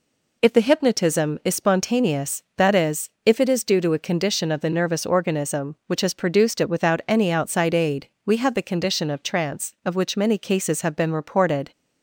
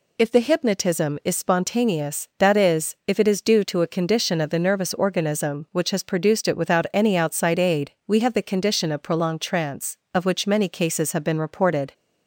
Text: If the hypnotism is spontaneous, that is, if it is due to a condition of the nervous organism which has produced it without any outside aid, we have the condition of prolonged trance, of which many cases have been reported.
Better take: second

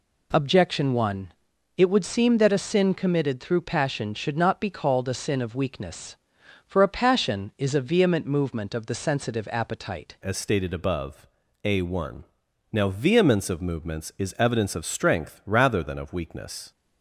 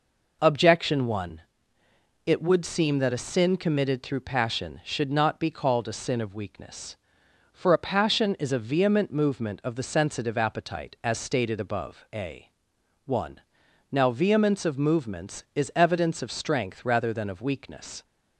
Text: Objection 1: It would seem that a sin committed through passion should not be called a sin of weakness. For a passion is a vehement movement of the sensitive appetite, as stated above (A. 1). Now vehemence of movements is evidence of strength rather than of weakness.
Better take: second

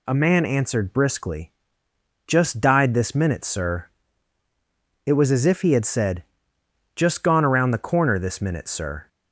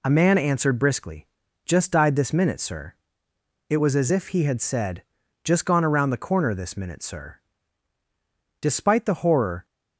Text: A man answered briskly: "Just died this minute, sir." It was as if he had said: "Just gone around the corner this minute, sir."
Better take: first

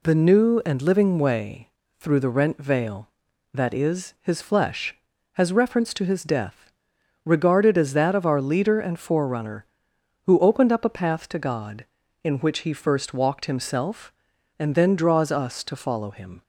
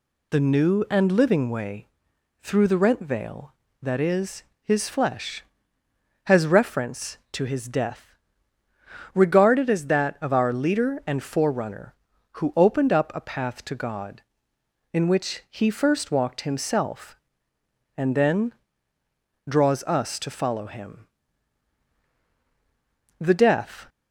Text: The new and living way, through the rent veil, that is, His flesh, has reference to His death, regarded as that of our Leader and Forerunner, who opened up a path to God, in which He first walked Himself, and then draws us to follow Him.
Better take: first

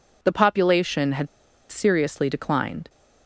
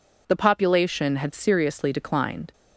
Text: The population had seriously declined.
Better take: second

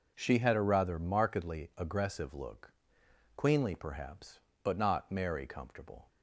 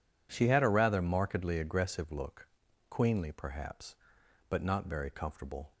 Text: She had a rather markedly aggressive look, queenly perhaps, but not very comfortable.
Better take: second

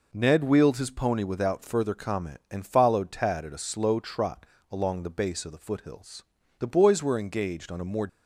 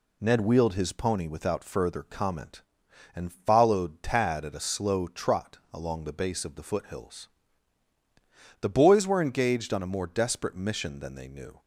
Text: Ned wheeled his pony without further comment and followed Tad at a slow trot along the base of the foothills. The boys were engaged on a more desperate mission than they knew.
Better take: second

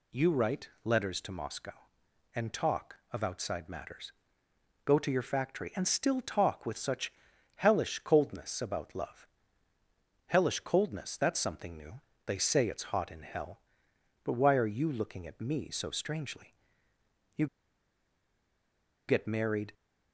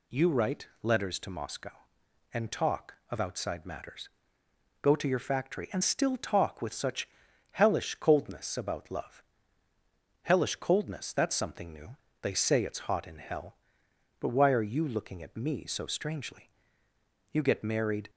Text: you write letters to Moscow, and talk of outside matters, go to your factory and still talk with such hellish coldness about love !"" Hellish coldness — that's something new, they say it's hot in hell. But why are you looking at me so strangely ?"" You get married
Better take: second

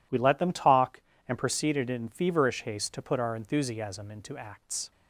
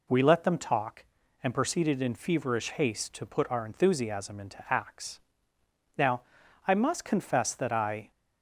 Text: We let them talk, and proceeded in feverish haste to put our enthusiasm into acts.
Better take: first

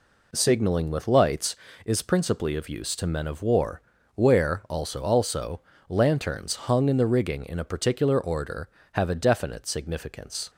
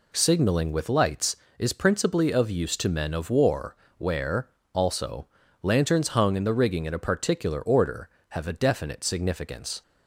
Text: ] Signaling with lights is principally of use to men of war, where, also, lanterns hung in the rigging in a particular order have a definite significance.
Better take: second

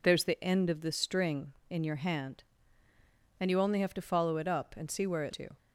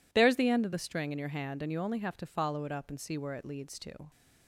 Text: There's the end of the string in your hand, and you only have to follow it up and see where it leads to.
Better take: second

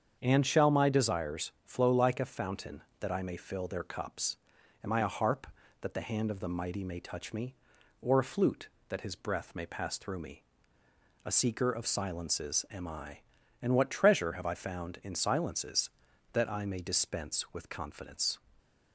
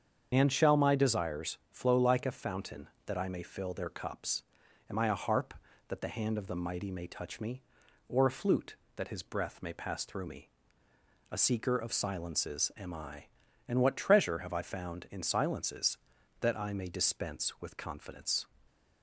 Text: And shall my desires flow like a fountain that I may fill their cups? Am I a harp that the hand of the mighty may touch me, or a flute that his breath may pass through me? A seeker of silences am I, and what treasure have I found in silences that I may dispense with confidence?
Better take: first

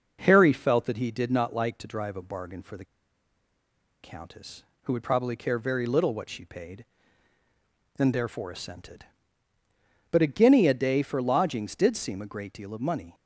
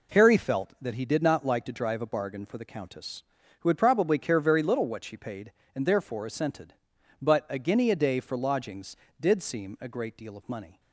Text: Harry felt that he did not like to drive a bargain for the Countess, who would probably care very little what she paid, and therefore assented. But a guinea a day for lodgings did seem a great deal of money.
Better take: second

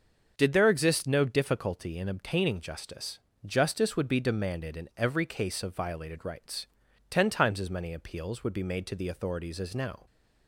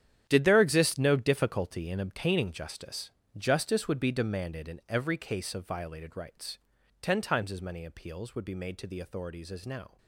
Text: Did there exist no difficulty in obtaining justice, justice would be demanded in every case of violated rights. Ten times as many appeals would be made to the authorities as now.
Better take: first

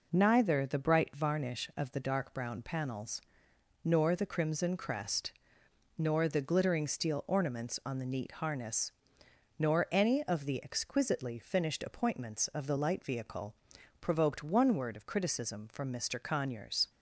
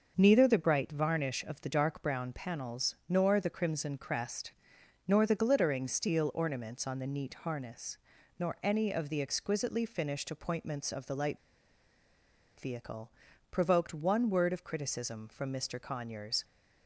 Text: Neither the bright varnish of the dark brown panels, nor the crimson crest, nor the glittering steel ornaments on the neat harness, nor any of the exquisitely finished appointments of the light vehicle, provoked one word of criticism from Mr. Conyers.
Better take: first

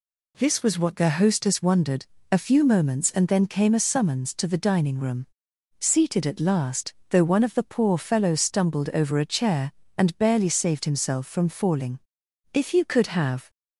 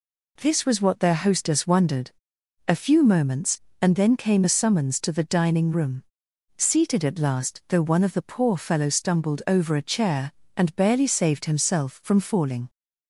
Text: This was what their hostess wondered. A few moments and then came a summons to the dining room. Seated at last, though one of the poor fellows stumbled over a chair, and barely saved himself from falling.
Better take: second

